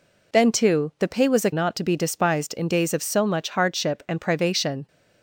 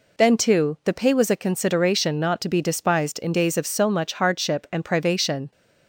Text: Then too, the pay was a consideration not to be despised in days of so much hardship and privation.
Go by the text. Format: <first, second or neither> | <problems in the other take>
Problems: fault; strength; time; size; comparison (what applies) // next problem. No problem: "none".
second | skips "consideration"; at 1.5 s